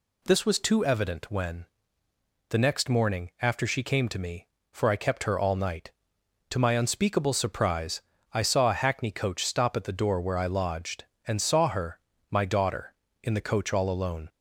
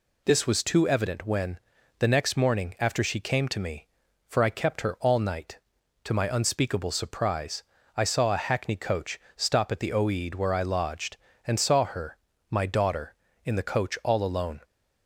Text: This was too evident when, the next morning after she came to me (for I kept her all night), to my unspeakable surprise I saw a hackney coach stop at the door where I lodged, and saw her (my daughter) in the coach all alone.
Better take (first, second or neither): first